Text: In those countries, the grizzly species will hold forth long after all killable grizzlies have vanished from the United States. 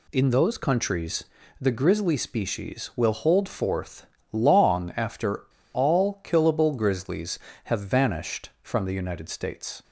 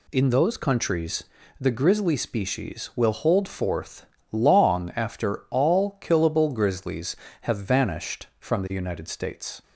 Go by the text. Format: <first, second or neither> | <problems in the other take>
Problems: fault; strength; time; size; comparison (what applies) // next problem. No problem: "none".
second | pauses between "forth" and "long"; slight; at 4.0 s; 0.26 s long; slight in the second // pauses between "after" and "all"; slight; at 5.4 s; 0.31 s long